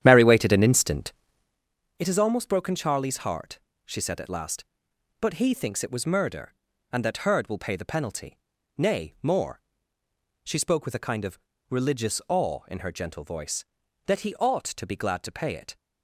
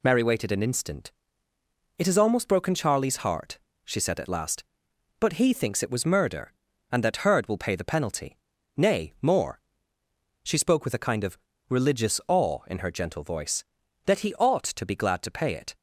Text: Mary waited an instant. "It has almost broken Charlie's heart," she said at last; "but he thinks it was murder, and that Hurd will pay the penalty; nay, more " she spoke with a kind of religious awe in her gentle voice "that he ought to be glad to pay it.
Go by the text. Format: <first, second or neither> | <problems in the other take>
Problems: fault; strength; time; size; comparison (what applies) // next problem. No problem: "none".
second | starts louder than the rest; strong; until 1.7 s; 10.5 dB // pauses between "of" and "religious"; slight; at 11.3 s; 0.32 s long; slight in the second